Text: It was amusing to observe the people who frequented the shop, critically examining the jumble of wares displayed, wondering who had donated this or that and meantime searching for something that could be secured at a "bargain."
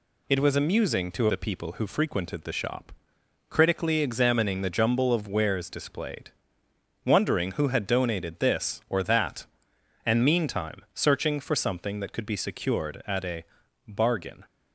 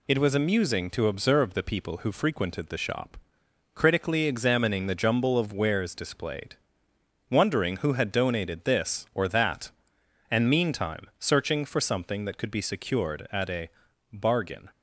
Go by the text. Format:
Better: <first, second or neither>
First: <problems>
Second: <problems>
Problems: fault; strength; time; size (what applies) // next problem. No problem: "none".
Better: second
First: skips "observe"; at 1.2 s // pauses between "a" and "bargain"; at 13.4 s; 0.44 s long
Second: pauses between "a" and "bargain"; at 13.6 s; 0.44 s long